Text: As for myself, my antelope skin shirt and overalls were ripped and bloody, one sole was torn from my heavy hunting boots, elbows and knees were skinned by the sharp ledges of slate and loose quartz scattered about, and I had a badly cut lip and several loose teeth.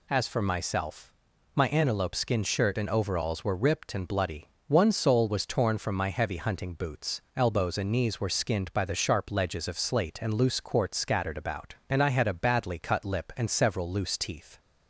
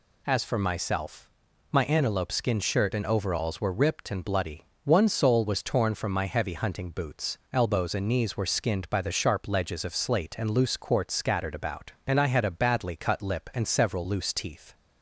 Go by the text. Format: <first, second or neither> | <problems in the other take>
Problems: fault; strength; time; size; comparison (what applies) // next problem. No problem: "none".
neither | none